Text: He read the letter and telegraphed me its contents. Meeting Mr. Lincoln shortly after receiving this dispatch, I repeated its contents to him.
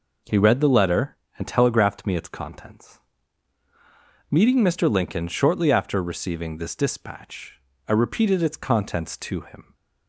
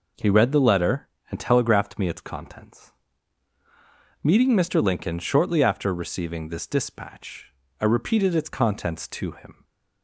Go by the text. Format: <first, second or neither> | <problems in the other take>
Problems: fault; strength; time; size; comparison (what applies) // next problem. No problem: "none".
neither | none